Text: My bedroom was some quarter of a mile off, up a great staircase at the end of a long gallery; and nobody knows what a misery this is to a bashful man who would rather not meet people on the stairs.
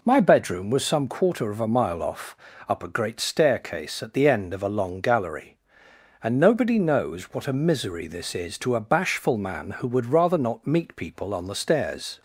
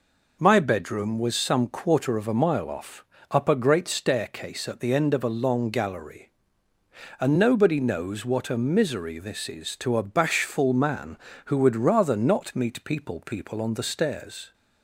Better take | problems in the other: first | says "people" twice; at 13.2 s

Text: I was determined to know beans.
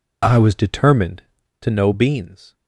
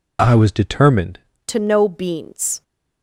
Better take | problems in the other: first | changes voice at "to"; from 1.4 s on; 1.2 s long

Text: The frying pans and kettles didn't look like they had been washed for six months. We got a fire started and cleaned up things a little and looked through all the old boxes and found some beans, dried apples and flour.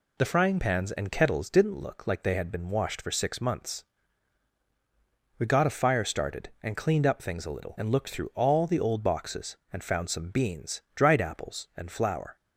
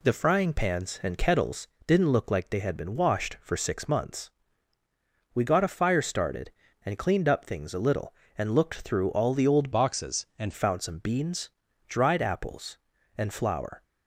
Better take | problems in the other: first | pauses between "kettles" and "didn't"; slight; at 1.6 s; 0.18 s long // changes voice from "boxes" to "and"; from 9.7 to 10.5 s; 0.8 s long

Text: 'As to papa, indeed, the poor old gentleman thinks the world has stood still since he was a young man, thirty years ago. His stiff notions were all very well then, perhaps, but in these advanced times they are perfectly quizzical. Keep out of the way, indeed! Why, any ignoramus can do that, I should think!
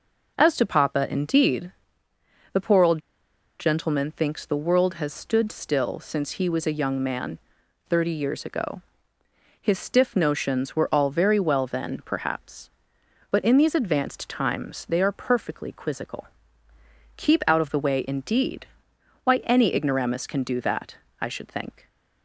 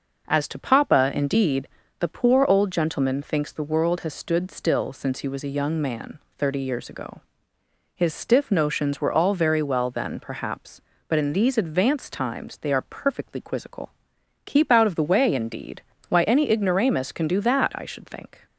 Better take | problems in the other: second | pauses between "old" and "gentleman"; noticeable; at 3.0 s; 0.59 s long

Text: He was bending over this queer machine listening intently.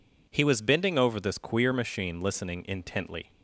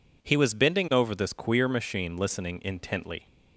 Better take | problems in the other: neither | none

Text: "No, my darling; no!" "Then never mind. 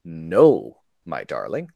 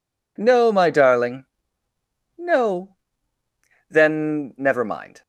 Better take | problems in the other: second | stops before "no Then never mind"; at 1.7 s

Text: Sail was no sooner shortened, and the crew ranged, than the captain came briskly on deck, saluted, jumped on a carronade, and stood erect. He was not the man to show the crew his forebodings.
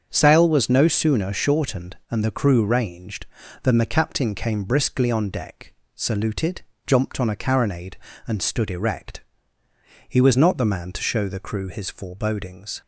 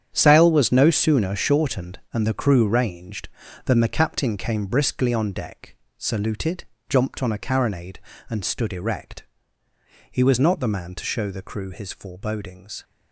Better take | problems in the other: first | gets quieter; strong; throughout; 12 dB // starts louder than the rest; strong; until 1.1 s; 8.5 dB; also in the first

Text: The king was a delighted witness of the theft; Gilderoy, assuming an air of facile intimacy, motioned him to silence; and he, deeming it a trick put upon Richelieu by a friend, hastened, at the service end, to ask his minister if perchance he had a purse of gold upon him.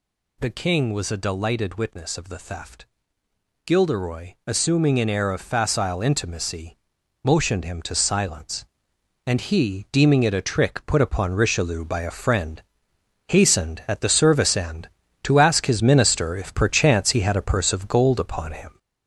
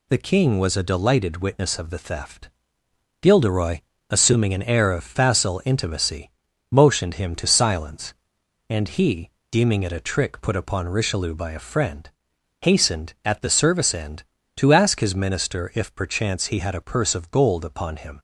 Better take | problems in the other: second | gets louder; noticeable; throughout; 4.5 dB

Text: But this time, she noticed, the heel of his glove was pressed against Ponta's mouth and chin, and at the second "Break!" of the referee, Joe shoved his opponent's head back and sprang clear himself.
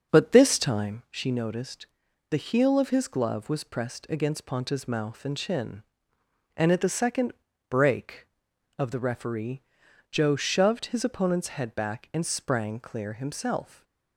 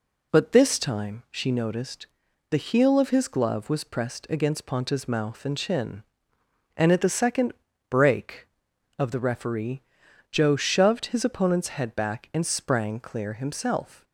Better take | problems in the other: second | starts louder than the rest; until 1.1 s; 6.5 dB // pauses between "second" and "Break"; at 7.3 s; 0.38 s long; also in the second // stays silent after the last word; slight; from 13.6 s on; 0.5 s long

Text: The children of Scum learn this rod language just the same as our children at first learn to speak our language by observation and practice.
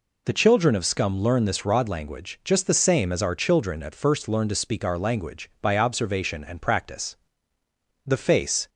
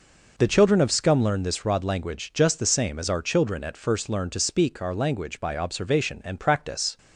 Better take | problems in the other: second | goes on to say "The face"; noticeable; from 8.0 s on; 0.62 s long

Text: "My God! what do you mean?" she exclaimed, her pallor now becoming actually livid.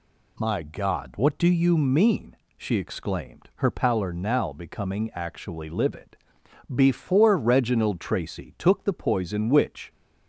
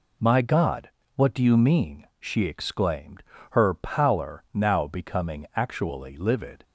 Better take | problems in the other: second | goes on to say "Before Reginald Tracy took the poison which"; strong; from 6.7 s on; 3.1 s long

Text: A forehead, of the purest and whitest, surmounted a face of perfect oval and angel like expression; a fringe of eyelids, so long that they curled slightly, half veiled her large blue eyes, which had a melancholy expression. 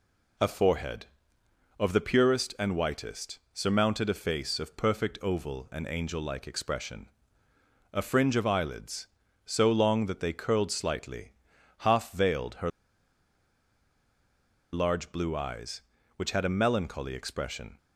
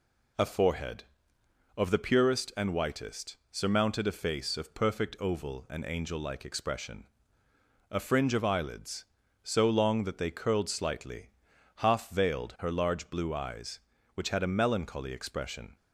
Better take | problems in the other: second | pauses between "her" and "large"; strong; at 12.6 s; 2.0 s long

